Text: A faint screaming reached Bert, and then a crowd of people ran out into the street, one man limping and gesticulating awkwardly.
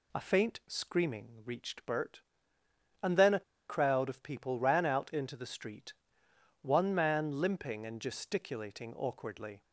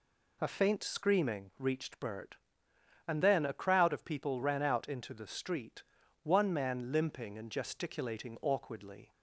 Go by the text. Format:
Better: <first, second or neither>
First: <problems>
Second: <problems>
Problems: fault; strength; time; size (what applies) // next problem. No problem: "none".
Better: second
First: pauses between "a" and "crowd"; slight; at 3.4 s; 0.27 s long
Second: none